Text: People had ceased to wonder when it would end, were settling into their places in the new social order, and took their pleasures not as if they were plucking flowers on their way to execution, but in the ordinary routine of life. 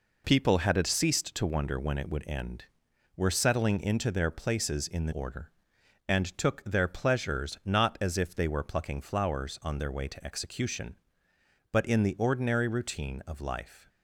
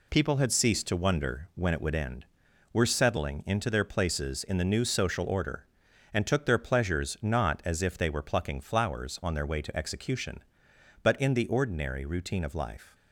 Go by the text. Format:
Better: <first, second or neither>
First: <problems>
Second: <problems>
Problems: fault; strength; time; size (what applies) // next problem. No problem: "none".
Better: second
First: skips "new social"; at 5.1 s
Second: none